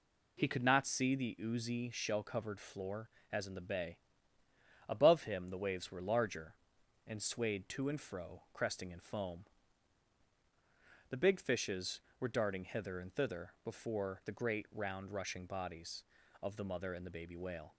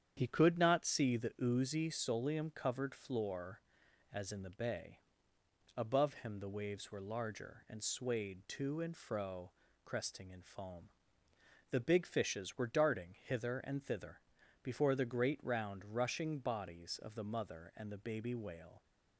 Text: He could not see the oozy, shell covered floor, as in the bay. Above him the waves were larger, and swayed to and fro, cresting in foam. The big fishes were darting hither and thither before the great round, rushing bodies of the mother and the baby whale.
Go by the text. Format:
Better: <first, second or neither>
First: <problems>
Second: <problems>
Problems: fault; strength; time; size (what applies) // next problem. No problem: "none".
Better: first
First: none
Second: starts louder than the rest; strong; until 1.1 s; 8.5 dB // says "solium" for "shell"; at 1.8 s // pauses between "thither" and "before"; at 14.1 s; 0.44 s long